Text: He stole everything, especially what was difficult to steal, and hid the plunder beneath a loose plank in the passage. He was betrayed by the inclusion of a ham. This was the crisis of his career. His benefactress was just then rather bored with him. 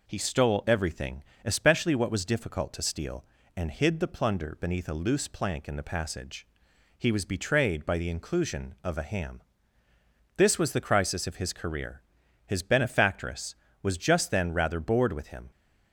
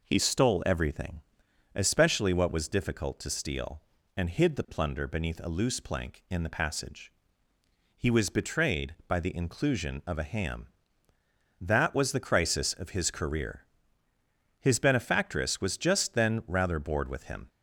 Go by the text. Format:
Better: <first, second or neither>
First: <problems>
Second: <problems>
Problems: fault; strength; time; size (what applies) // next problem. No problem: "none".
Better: first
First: none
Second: says "That" for "This"; at 11.6 s